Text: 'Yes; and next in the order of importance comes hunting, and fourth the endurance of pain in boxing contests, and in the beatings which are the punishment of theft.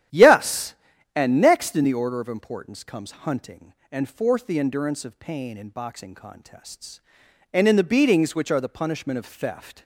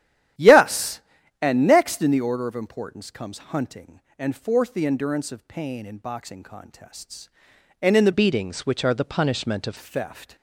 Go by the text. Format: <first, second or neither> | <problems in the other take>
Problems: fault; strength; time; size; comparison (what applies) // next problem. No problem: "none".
first | starts louder than the rest; strong; until 1.7 s; 11.5 dB; strong in the first // changes voice from "beatings" to "of"; from 8.1 to 9.7 s; 1.6 s long